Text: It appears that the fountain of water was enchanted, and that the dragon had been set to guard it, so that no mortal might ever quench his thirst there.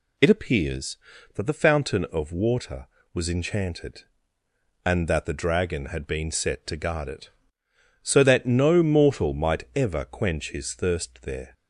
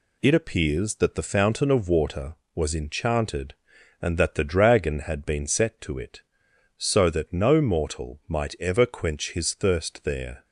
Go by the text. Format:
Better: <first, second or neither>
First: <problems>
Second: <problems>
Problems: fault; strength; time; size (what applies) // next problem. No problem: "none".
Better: first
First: none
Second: skips "guard"; at 5.9 s